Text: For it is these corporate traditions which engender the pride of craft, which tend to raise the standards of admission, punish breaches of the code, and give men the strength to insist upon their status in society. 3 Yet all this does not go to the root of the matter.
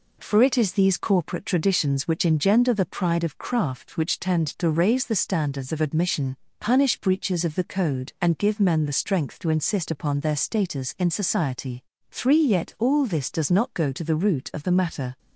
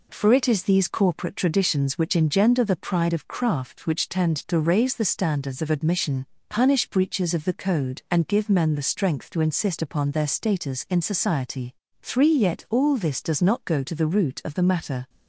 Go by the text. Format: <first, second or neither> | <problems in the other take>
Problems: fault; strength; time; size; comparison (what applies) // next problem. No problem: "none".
neither | none